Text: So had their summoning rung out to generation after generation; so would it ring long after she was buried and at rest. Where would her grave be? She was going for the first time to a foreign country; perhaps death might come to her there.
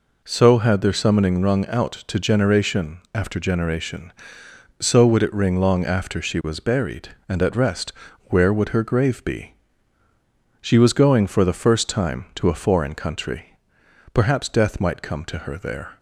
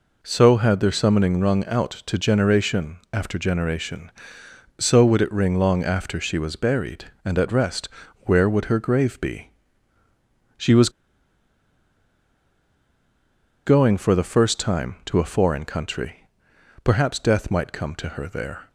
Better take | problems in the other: first | pauses between "was" and "going"; strong; at 10.8 s; 2.7 s long

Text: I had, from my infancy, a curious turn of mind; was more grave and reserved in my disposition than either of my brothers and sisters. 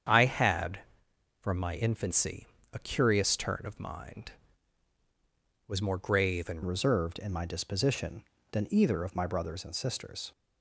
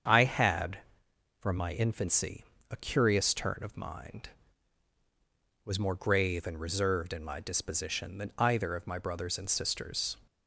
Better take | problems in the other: second | starts louder than the rest; strong; until 1.7 s; 8 dB; strong in the second // changes voice at "reserved"; from 6.6 s on; 3.7 s long

